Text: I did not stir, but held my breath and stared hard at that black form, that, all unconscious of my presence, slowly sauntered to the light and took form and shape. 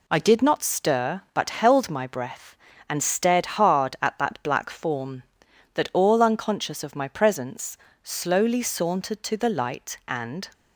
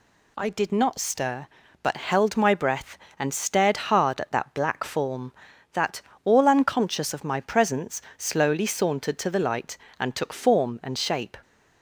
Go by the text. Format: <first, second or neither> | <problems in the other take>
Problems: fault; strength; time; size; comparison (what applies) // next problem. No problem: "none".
second | stops before "took form and shape"; at 10.5 s